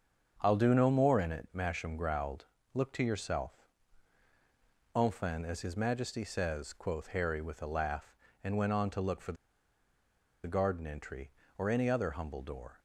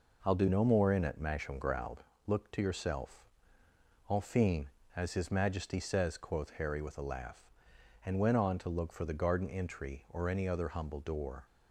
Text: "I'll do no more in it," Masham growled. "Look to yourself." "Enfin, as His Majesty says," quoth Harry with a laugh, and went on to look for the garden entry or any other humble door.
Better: second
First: starts louder than the rest; strong; until 1.4 s; 7 dB // pauses between "the" and "garden"; at 9.3 s; 1.1 s long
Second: none

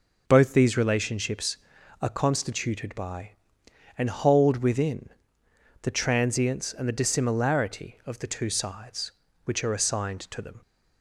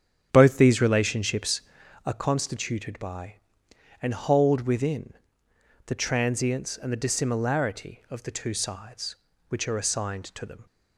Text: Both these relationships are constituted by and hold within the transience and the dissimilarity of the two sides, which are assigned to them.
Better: first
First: pauses between "within" and "the"; noticeable; at 5.0 s; 0.72 s long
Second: starts louder than the rest; strong; until 2.0 s; 9 dB // pauses between "within" and "the"; noticeable; at 5.1 s; 0.72 s long

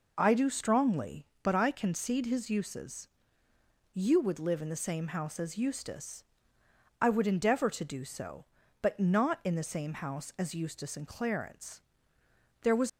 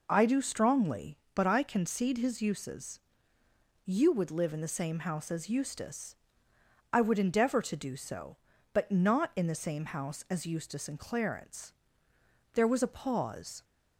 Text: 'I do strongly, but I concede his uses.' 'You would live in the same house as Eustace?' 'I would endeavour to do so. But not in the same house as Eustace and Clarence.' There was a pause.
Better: second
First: stops before "a pause"; at 12.8 s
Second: none

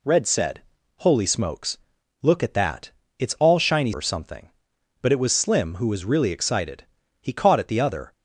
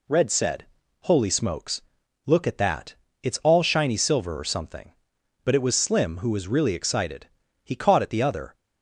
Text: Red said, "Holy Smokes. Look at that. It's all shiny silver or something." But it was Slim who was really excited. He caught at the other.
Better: second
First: skips "silver"; at 3.9 s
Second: none

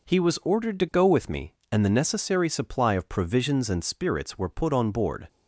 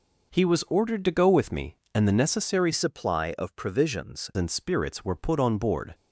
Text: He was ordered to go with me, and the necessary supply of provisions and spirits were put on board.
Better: first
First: none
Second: changes voice from "supply" to "provisions"; from 2.7 to 4.2 s; 1.5 s long

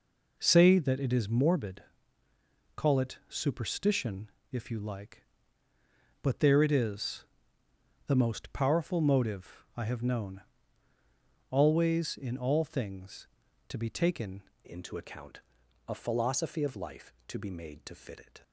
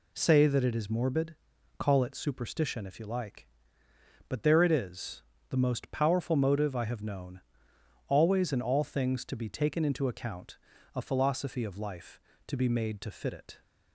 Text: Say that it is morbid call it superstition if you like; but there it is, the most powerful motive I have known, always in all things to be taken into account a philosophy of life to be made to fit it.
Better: second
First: pauses between "morbid" and "call"; noticeable; at 1.8 s; 0.94 s long // pauses between "superstition" and "if"; slight; at 4.2 s; 0.22 s long // changes voice at "into"; from 14.6 s on; 3.8 s long // pauses between "account" and "a"; noticeable; at 15.3 s; 0.48 s long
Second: pauses between "morbid" and "call"; at 1.3 s; 0.44 s long // pauses between "account" and "a"; at 10.5 s; 0.36 s long

